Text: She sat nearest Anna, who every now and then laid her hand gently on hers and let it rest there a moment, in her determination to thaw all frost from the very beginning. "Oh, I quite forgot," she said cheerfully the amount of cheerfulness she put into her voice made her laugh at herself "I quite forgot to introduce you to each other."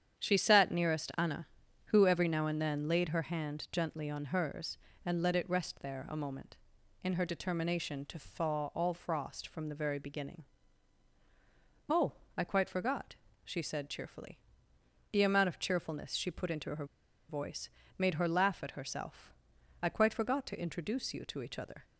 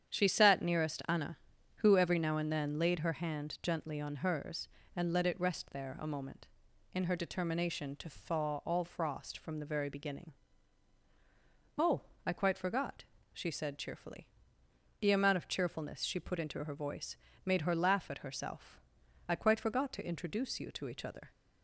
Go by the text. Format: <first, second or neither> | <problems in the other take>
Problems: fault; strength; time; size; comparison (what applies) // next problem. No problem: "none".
second | starts louder than the rest; strong; until 1.2 s; 8.5 dB; strong in the second // pauses between "cheerfully" and "the"; noticeable; at 14.3 s; 0.72 s long; noticeable in the second // pauses between "her" and "voice"; at 16.8 s; 0.44 s long // pauses between "voice" and "made"; slight; at 17.7 s; 0.26 s long; slight in the second // pauses between "herself" and "I"; noticeable; at 19.3 s; 0.48 s long; noticeable in the second